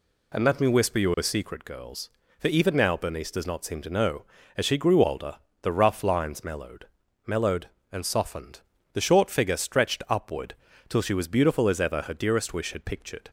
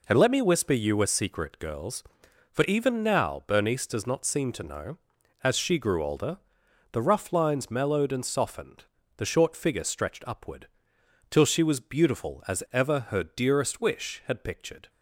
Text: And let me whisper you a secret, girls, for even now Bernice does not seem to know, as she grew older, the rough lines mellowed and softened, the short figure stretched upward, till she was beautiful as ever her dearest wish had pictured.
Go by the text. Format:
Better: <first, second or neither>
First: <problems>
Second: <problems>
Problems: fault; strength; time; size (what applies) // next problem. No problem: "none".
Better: second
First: says "mellowed" twice; at 7.2 s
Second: none